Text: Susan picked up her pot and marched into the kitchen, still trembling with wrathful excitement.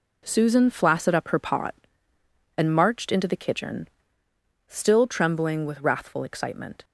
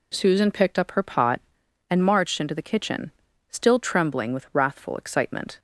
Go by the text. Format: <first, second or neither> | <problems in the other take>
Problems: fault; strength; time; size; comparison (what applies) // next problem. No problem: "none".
second | says "flaccid" for "picked"; at 0.6 s